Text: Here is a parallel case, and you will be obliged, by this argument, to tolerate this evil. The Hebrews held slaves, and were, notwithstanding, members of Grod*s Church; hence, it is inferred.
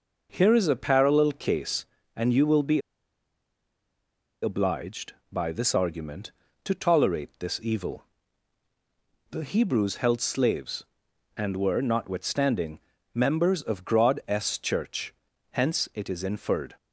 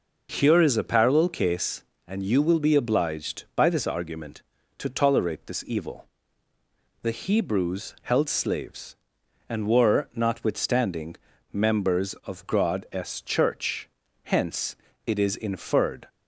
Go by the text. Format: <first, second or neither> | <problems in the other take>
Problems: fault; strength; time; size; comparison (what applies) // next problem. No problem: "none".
second | pauses between "be" and "obliged"; strong; at 2.7 s; 1.6 s long